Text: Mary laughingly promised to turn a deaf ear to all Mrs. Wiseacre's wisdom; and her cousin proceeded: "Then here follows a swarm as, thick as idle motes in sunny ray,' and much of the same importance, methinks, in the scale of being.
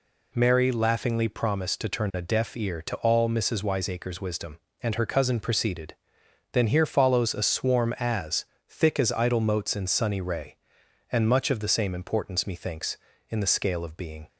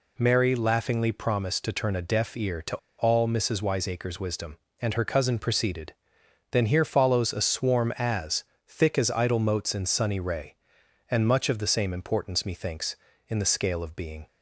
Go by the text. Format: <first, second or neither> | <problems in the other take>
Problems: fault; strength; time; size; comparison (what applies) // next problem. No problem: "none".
first | pauses between "to" and "all"; slight; at 2.7 s; 0.22 s long